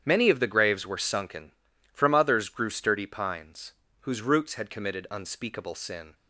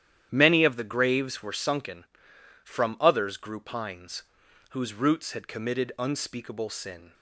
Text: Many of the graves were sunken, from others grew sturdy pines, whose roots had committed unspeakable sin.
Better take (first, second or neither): first